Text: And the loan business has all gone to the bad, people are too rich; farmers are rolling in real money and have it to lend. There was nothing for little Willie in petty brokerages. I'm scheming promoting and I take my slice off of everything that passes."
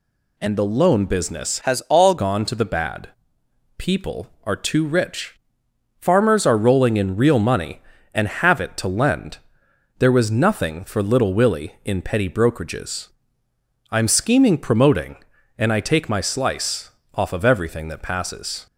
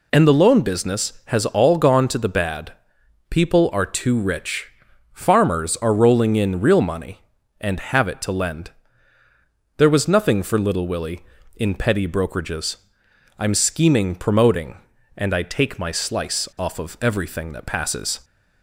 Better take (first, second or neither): second